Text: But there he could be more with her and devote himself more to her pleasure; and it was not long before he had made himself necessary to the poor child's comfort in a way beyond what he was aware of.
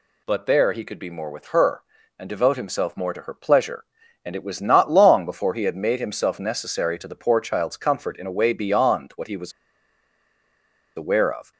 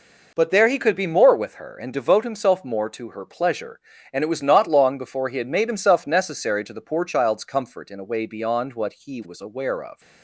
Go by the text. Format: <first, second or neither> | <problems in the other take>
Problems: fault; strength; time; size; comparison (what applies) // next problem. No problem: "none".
second | pauses between "was" and "aware"; strong; at 9.5 s; 1.4 s long